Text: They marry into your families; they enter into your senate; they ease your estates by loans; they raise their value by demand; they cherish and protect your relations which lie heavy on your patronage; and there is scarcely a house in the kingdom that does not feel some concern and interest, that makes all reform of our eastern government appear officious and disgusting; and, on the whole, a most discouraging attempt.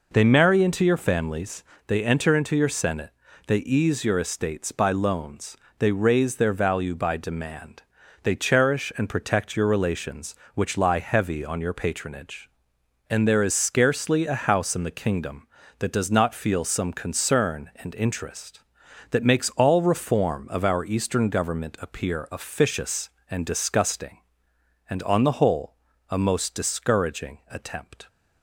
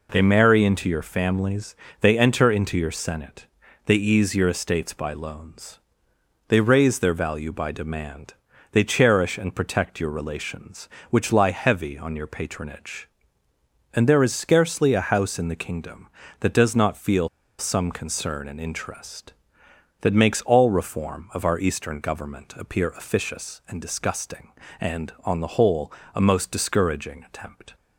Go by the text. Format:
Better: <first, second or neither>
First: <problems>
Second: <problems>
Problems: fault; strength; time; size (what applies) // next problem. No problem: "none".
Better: first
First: none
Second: pauses between "feel" and "some"; slight; at 17.2 s; 0.30 s long